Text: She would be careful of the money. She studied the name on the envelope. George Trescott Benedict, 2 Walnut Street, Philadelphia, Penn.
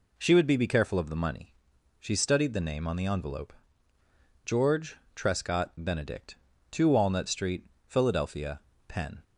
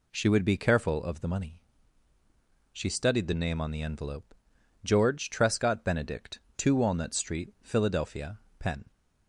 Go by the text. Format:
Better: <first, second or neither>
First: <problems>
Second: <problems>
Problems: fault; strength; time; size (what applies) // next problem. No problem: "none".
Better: second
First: says "be" twice; at 0.5 s // pauses between "George" and "Trescott"; slight; at 4.9 s; 0.18 s long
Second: none